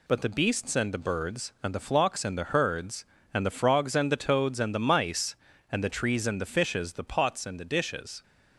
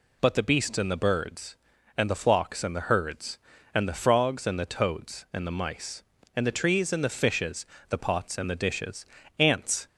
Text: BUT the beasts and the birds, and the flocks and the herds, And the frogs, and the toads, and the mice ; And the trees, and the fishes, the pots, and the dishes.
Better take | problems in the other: first | goes on to say "Ants"; slight; from 9.3 s on; 0.48 s long

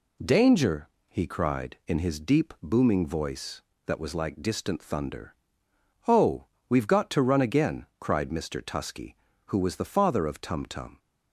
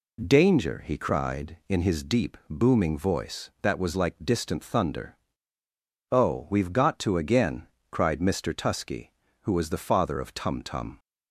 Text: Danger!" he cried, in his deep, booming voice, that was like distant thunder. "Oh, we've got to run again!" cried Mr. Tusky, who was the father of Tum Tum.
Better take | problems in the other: first | skips "run"; at 7.1 s

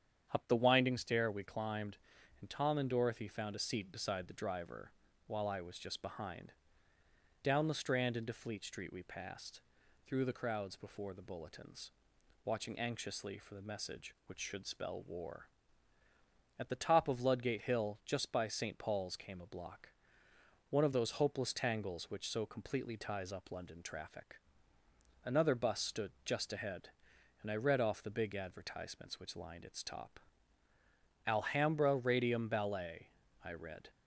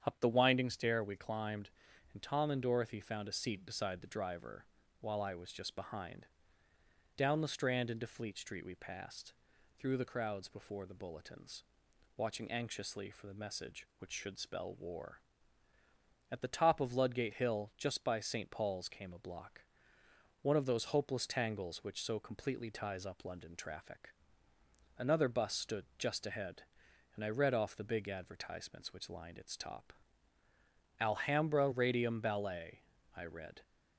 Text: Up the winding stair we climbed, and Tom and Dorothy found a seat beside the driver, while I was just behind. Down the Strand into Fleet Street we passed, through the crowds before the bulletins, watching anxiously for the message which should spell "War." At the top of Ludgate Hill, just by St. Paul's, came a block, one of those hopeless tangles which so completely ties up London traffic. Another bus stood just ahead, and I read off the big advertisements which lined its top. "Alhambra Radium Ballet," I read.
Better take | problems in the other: neither | starts louder than the rest; strong; the same in both

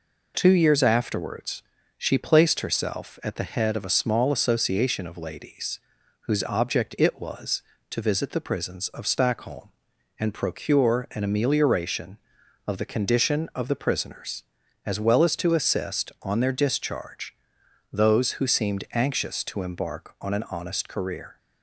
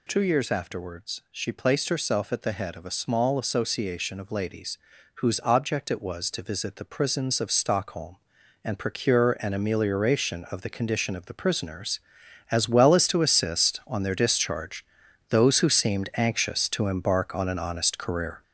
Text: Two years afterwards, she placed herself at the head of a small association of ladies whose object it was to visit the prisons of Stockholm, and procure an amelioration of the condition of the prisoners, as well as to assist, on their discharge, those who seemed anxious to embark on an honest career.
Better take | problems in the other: first | gets louder; noticeable; throughout; 5.5 dB // pauses between "ladies" and "whose"; at 4.7 s; 0.38 s long; also in the first

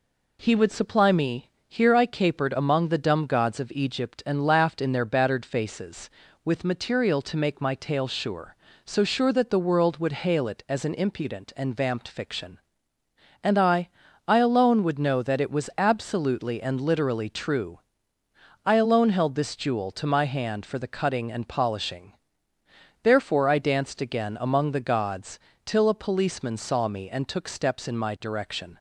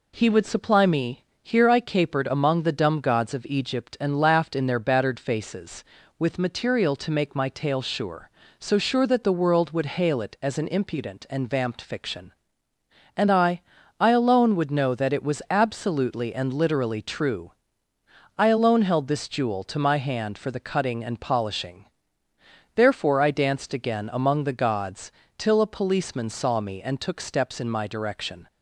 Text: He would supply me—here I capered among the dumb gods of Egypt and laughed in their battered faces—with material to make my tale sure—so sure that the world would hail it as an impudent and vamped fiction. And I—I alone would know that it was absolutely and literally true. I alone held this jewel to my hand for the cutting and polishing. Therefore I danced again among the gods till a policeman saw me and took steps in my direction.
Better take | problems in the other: neither | pauses between "gods" and "till"; slight; the same in both

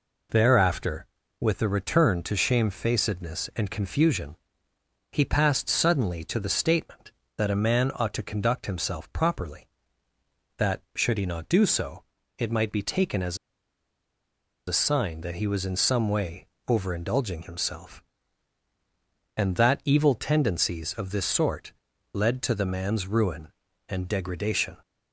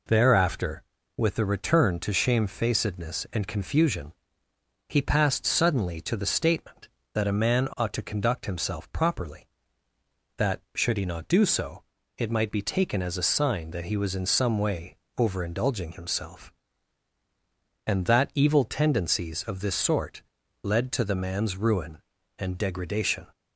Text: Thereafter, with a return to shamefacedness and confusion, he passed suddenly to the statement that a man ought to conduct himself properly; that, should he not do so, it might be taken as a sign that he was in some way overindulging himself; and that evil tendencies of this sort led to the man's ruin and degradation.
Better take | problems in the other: second | pauses between "as" and "a"; strong; at 13.3 s; 1.3 s long // pauses between "way" and "overindulging"; slight; at 16.4 s; 0.20 s long; slight in the second // pauses between "sort" and "led"; at 21.7 s; 0.40 s long; also in the second

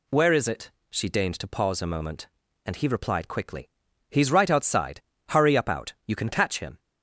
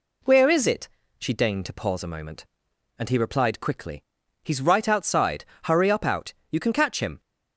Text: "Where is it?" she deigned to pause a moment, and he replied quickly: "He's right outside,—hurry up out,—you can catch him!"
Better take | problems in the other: neither | none

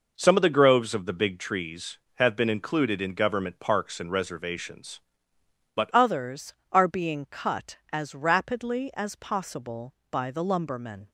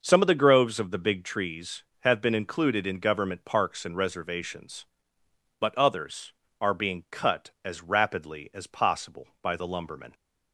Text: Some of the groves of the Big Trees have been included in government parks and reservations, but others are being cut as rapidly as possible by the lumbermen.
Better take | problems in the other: second | changes voice at "others"; from 5.9 s on; 5.1 s long

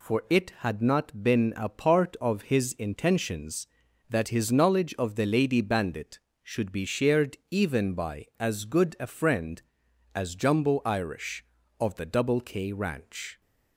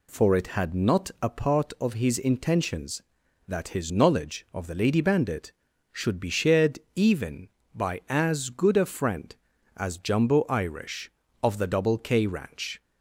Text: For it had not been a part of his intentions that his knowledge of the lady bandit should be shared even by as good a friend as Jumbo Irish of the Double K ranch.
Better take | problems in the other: first | skips "been"; at 1.1 s // pauses between "shared" and "even"; slight; at 6.7 s; 0.16 s long

